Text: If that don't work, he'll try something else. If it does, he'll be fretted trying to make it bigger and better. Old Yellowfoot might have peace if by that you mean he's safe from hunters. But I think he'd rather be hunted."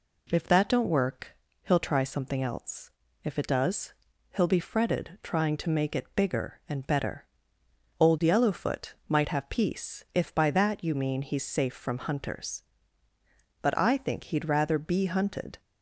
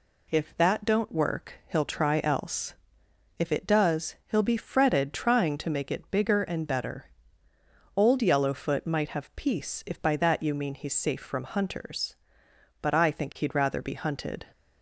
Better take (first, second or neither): first